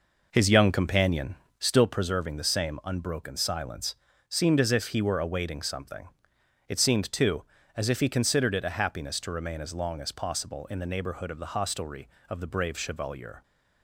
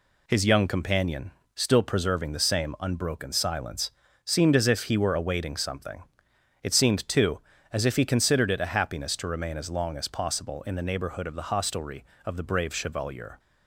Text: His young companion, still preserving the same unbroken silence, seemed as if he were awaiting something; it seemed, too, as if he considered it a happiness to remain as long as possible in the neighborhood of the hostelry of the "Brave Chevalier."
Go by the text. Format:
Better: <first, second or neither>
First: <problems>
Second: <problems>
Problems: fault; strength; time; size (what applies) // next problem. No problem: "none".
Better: second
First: starts louder than the rest; noticeable; until 2.0 s; 5 dB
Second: none